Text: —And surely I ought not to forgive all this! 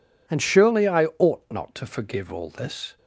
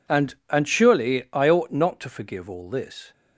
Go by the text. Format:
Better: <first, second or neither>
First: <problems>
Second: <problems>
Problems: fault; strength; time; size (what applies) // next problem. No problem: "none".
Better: first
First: none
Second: says "And" twice; at 0.5 s